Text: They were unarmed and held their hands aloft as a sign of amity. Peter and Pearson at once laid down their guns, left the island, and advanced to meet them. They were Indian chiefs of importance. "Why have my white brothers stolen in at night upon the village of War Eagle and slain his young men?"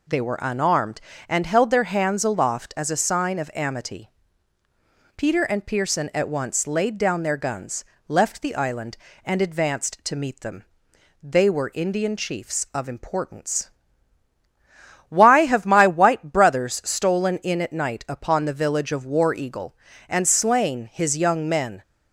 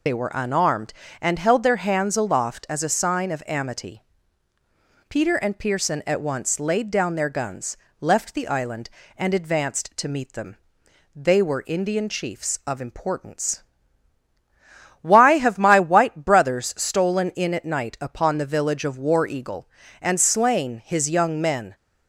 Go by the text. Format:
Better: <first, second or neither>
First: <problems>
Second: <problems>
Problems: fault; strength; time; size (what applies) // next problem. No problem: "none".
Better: first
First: none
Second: loses the start of "They"; at 0.0 s; 55 ms